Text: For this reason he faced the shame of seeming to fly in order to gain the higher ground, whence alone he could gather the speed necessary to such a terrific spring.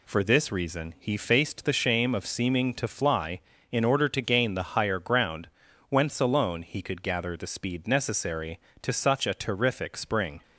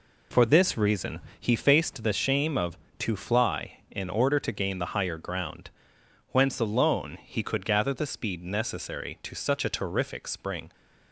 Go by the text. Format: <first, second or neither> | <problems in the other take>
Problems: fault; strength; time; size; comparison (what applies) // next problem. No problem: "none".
first | pauses between "reason" and "he"; slight; at 1.1 s; 0.18 s long // skips "seeming"; at 2.8 s